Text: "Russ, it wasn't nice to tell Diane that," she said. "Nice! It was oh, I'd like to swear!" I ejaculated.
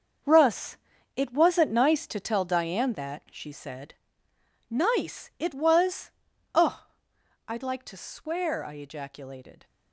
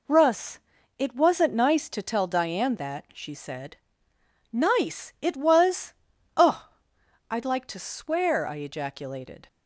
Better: second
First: gets quieter; strong; throughout; 11 dB // pauses between "was" and "oh"; at 6.1 s; 0.42 s long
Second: pauses between "was" and "oh"; at 5.9 s; 0.42 s long

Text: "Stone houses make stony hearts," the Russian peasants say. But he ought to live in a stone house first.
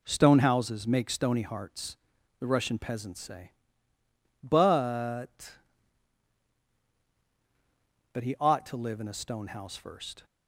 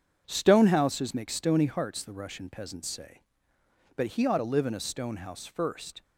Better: second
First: says "But" twice; at 8.1 s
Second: none

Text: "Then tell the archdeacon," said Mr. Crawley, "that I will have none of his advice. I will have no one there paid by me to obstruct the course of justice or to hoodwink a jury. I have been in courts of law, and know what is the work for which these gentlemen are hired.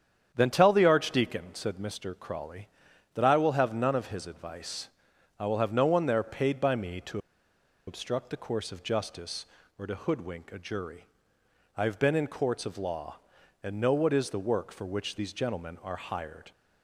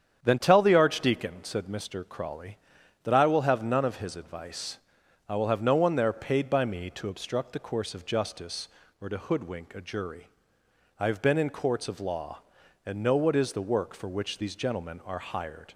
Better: second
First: starts louder than the rest; strong; until 1.3 s; 8.5 dB // pauses between "to" and "obstruct"; noticeable; at 7.1 s; 0.69 s long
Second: starts louder than the rest; strong; until 1.2 s; 8.5 dB

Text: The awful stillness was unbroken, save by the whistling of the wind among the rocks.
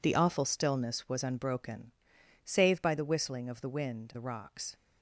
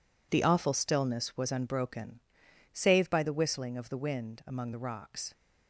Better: second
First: skips "among"; at 4.1 s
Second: none

